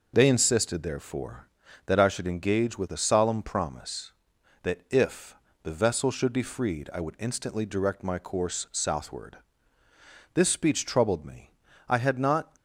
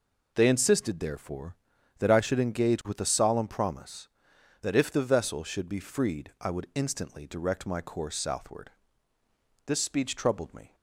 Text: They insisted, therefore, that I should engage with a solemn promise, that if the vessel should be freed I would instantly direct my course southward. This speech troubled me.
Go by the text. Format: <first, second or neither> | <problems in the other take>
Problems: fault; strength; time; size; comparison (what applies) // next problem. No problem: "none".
second | pauses between "if" and "the"; slight; at 5.3 s; 0.28 s long // goes on to say "I had not"; noticeable; from 11.8 s on; 0.66 s long